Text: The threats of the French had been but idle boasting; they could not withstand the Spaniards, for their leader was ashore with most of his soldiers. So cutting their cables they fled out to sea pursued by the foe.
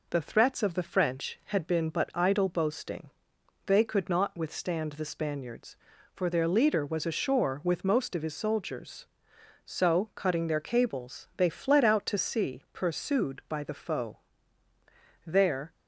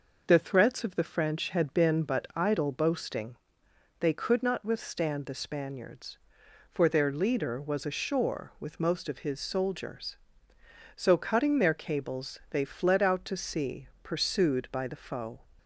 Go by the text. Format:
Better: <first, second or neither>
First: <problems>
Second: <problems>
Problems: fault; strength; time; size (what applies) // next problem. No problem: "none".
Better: second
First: goes on to say "There"; slight; from 15.2 s on; 0.46 s long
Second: none